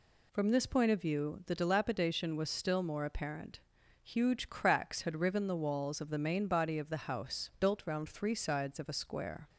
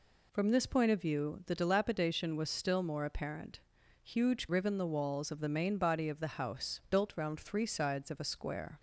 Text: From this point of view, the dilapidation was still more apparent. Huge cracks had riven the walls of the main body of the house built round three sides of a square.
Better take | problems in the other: first | skips "cracks had"; at 4.4 s

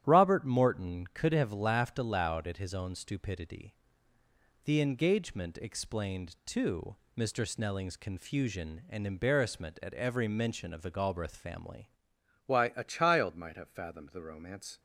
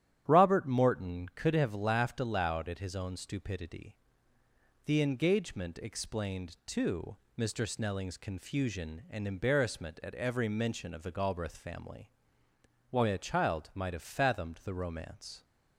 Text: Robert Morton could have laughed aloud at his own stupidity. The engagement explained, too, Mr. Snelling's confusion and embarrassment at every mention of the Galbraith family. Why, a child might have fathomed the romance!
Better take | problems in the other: second | starts louder than the rest; strong; until 1.0 s; 10 dB; strong in the second // changes voice at "Why"; from 12.4 s on; 2.3 s long

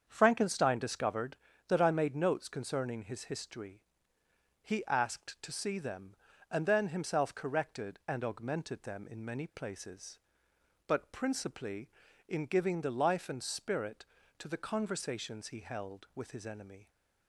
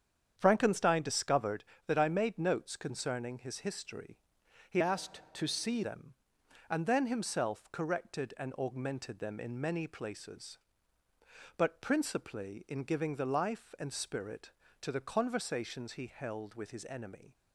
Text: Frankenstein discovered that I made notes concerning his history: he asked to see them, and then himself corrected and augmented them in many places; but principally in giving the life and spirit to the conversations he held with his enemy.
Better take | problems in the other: first | starts louder than the rest; strong; until 1.3 s; 8 dB; strong in the first // changes voice from "asked" to "see"; from 4.8 to 5.8 s; 1.0 s long

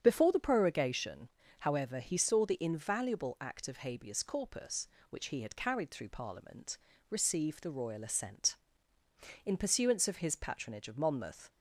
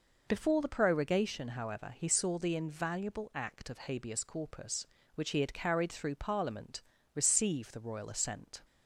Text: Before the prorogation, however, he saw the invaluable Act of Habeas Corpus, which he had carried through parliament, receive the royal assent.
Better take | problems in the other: second | starts louder than the rest; strong; until 1.0 s; 8 dB // goes on to say "In pursuance of his patronage of Monmouth"; strong; from 9.4 s on; 2.0 s long

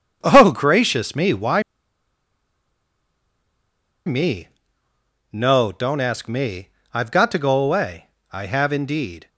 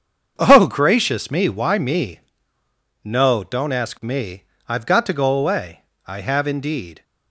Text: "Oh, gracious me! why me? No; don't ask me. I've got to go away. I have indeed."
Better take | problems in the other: second | starts louder than the rest; strong; until 1.2 s; 7.5 dB; strong in the second // pauses between "why" and "me"; strong; at 1.6 s; 2.4 s long

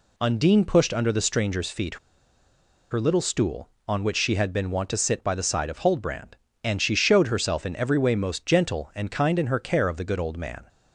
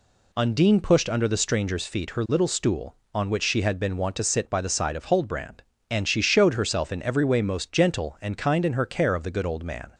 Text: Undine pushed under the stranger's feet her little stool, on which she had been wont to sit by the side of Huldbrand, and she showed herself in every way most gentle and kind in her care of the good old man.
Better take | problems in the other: second | pauses between "feet" and "her"; noticeable; at 1.9 s; 0.94 s long

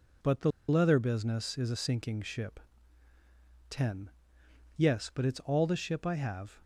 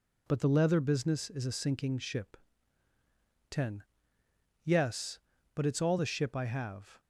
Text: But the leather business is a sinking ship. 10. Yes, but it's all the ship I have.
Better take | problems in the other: second | pauses between "the" and "leather"; slight; at 0.5 s; 0.19 s long

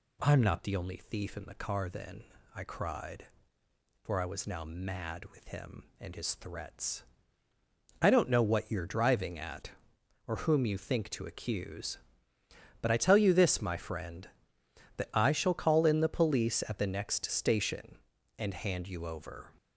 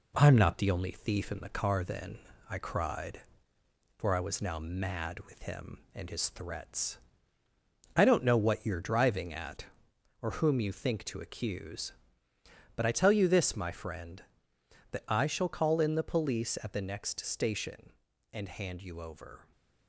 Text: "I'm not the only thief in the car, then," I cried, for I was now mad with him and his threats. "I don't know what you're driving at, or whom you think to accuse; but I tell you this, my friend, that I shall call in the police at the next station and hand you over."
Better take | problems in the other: first | gets quieter; slight; throughout; 2.5 dB

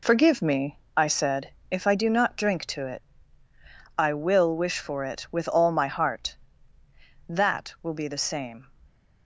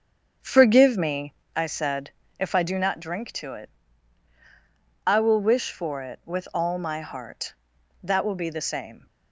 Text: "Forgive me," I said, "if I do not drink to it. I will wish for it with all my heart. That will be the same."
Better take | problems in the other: first | starts louder than the rest; strong; until 1.5 s; 7 dB

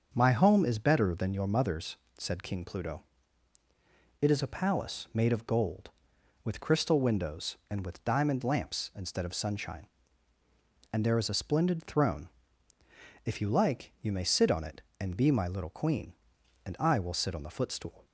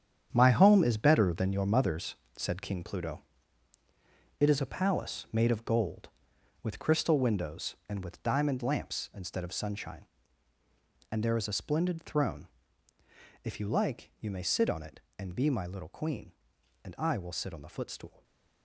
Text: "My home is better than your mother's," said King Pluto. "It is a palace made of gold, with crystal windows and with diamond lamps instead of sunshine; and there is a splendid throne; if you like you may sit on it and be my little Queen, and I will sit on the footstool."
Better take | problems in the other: first | gets quieter; strong; throughout; 10.5 dB // starts louder than the rest; strong; until 1.3 s; 8.5 dB; also in the first

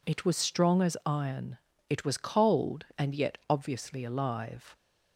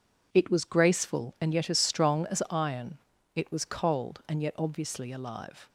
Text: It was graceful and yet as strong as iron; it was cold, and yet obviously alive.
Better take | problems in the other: second | skips "graceful and yet as"; at 0.3 s

